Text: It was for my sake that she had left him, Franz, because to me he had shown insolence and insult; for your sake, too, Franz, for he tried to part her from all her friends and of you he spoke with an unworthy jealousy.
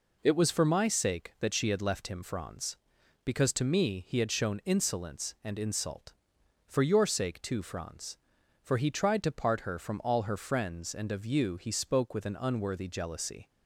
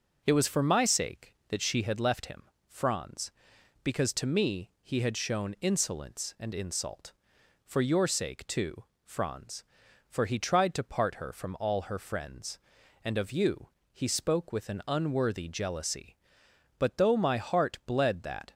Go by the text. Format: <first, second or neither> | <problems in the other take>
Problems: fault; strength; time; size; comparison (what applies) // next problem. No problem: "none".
first | pauses between "you" and "he"; slight; at 13.6 s; 0.22 s long // goes on to say "But though my heart bled that"; strong; from 16.7 s on; 1.7 s long